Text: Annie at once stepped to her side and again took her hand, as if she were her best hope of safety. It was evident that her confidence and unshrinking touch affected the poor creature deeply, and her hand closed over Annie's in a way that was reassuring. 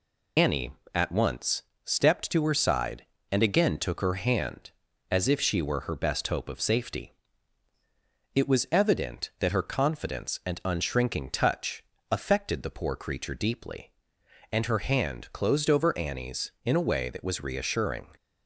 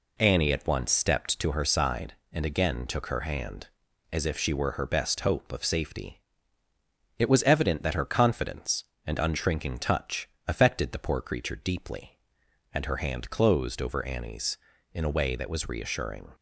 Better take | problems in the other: second | loses the start of "Annie"; at 0.3 s; 85 ms // pauses between "once" and "stepped"; slight; at 1.6 s; 0.22 s long // pauses between "touch" and "affected"; slight; at 11.8 s; 0.28 s long; slight in the second

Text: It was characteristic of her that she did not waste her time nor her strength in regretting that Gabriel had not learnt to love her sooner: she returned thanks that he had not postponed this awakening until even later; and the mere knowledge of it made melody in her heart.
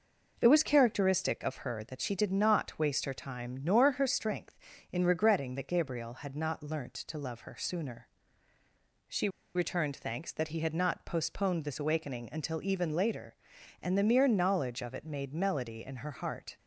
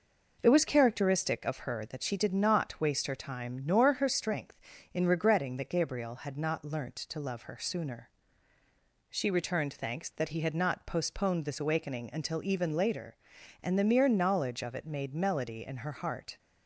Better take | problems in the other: second | pauses between "she" and "returned"; slight; at 9.2 s; 0.26 s long

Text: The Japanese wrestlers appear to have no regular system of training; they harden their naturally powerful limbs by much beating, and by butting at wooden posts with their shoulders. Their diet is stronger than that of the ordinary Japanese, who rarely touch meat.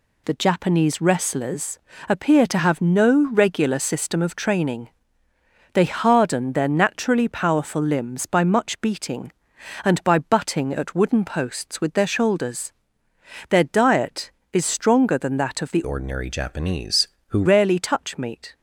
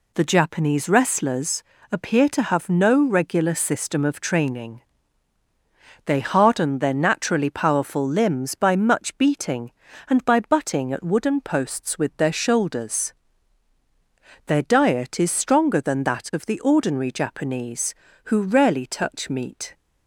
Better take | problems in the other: second | pauses between "wrestlers" and "appear"; slight; at 1.7 s; 0.30 s long; slight in the second // changes voice from "ordinary" to "who"; from 15.8 to 17.4 s; 1.6 s long

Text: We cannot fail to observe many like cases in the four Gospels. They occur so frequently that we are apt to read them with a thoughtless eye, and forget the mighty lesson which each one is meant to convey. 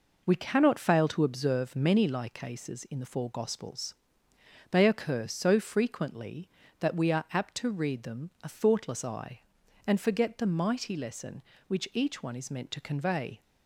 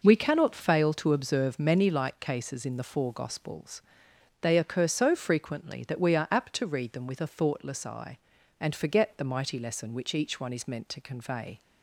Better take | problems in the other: second | skips "with"; at 8.3 s

